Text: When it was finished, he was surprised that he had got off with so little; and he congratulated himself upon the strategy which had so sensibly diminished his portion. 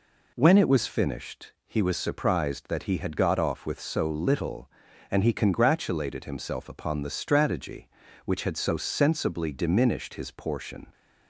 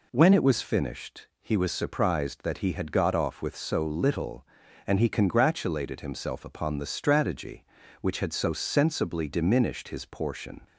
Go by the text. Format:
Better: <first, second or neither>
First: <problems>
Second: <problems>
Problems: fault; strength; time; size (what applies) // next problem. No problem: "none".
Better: neither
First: none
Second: none